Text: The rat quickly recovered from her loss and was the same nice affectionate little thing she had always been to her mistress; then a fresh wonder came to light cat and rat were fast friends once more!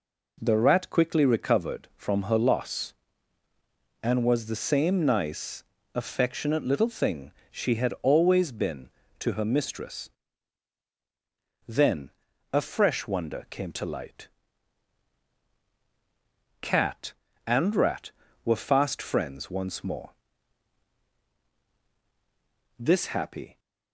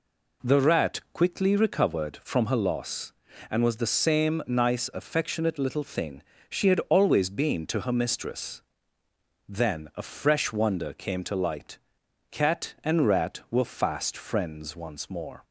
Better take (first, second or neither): second